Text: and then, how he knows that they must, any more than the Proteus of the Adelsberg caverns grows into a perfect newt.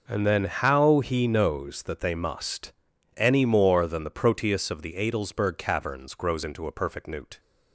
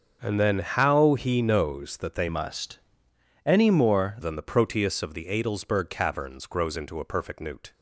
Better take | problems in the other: first | starts louder than the rest; until 1.2 s; 6.5 dB // changes voice from "must" to "more"; from 2.2 to 4.1 s; 1.9 s long

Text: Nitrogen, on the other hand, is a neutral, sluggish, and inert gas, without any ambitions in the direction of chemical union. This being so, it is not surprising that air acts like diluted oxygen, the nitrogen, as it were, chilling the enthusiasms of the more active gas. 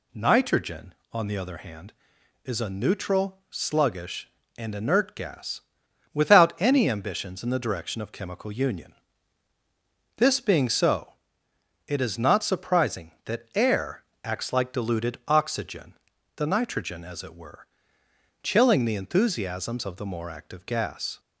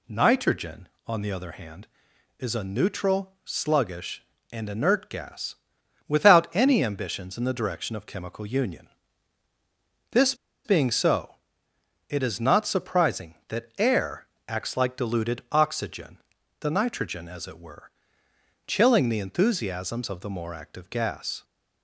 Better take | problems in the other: first | pauses between "This" and "being"; slight; at 10.3 s; 0.30 s long // pauses between "air" and "acts"; slight; at 14.2 s; 0.22 s long; slight in the first

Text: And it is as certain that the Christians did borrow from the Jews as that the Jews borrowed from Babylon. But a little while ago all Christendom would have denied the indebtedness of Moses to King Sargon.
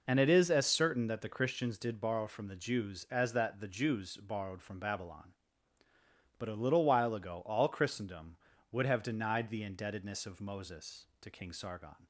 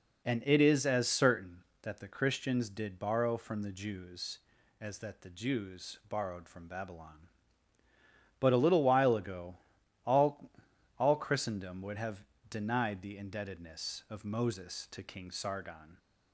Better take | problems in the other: first | pauses between "ago" and "all"; noticeable; at 9.5 s; 0.50 s long // says "all" twice; at 10.9 s // pauses between "have" and "denied"; slight; at 12.2 s; 0.27 s long

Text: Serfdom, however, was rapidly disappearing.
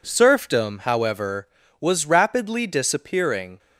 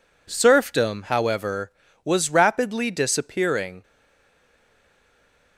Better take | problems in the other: first | stays silent after the last word; noticeable; from 3.8 s on; 1.7 s long

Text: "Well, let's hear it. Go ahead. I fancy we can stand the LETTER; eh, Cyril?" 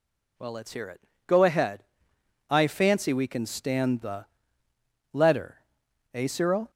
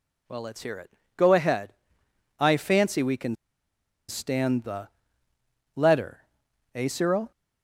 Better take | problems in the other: first | pauses between "can" and "stand"; noticeable; at 3.3 s; 0.73 s long // pauses between "the" and "LETTER"; noticeable; at 4.8 s; 0.86 s long; noticeable in the first

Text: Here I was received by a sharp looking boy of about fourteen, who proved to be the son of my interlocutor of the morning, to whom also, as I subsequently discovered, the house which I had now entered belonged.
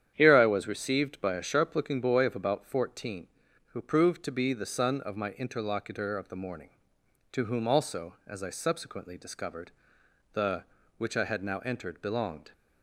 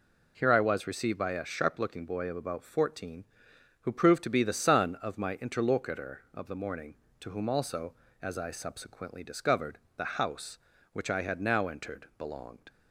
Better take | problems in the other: second | starts louder than the rest; strong; until 1.1 s; 9.5 dB // skips "house"; at 10.7 s

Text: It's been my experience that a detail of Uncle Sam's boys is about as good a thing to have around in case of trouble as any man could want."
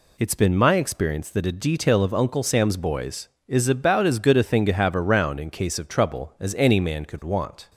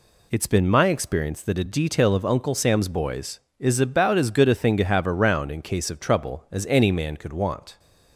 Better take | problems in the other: neither | none

